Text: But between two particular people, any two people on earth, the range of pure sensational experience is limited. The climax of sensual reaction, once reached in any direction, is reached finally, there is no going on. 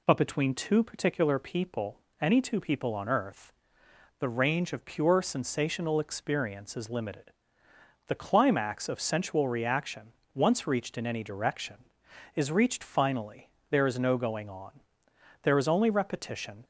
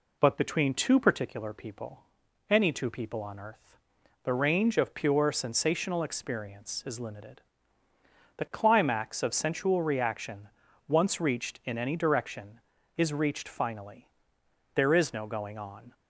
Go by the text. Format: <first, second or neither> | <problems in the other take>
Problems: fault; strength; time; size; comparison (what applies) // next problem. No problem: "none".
second | goes on to say "There is only repetition"; noticeable; from 15.4 s on; 1.2 s long